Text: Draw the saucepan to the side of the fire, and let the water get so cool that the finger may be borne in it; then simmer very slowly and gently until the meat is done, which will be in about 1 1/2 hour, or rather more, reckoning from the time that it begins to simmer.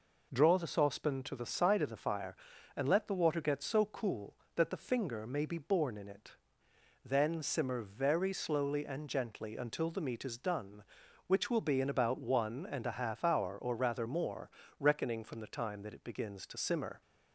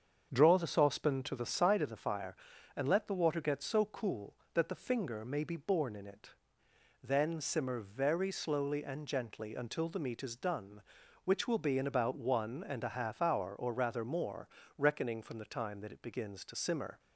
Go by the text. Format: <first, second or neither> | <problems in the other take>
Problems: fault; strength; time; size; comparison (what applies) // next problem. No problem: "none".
first | starts louder than the rest; strong; until 1.8 s; 7 dB